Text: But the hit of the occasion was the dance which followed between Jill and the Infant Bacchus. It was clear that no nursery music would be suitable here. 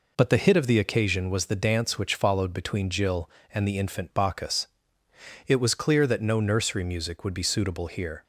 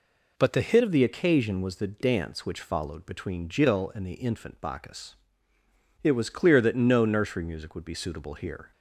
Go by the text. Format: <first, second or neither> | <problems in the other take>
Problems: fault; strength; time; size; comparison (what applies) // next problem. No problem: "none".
first | changes voice at "of"; from 0.8 s on; 7.9 s long